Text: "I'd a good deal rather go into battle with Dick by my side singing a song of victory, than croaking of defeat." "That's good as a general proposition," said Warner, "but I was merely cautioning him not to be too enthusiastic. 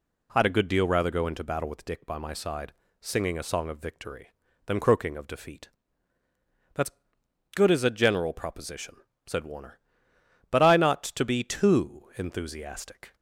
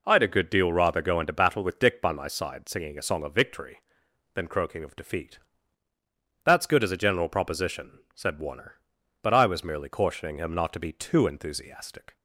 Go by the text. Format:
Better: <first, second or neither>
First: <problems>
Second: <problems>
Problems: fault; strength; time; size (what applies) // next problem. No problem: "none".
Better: second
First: pauses between "side" and "singing"; slight; at 2.7 s; 0.30 s long // pauses between "That's" and "good"; noticeable; at 6.9 s; 0.64 s long // skips "was merely cautioning him"; at 10.7 s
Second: none